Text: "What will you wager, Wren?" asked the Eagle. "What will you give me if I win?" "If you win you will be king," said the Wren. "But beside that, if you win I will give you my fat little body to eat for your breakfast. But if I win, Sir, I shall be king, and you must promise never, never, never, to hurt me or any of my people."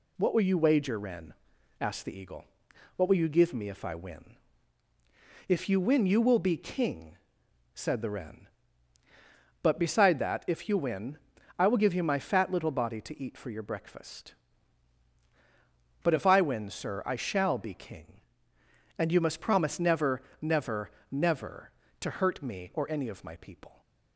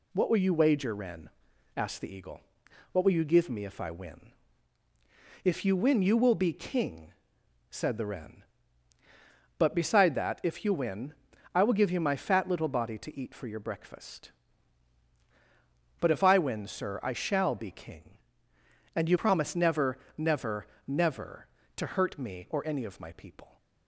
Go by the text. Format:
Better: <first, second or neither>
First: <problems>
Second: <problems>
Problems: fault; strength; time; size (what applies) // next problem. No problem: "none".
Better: first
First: pauses between "win" and "I"; at 11.1 s; 0.40 s long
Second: pauses between "win" and "I"; at 11.1 s; 0.40 s long // skips "must"; at 19.1 s